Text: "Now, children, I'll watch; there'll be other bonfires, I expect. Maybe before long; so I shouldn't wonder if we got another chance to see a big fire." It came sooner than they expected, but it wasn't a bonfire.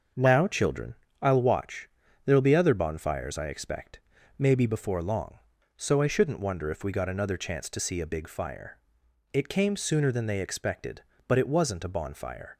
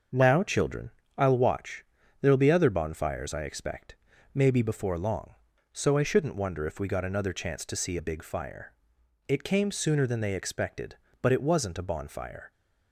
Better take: neither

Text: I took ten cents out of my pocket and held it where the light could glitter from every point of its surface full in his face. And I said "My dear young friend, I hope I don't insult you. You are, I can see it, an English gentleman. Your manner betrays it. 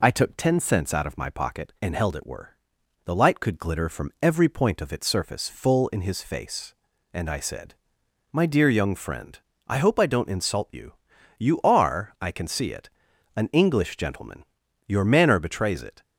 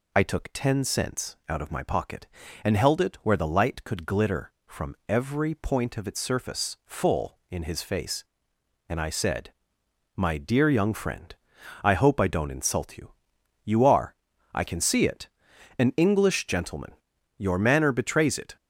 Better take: second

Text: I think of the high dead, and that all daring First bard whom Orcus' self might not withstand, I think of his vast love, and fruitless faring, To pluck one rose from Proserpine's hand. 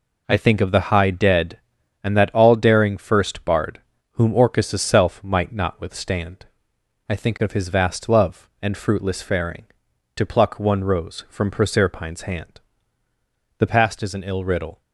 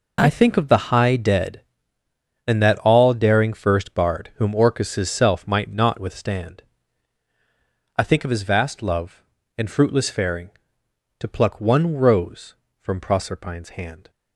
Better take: second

